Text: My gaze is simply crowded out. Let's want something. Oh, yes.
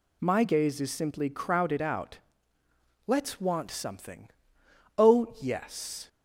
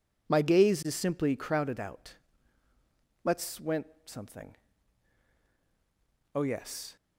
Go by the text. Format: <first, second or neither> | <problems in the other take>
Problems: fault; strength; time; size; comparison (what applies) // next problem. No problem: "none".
first | says "went" for "want"; at 3.5 s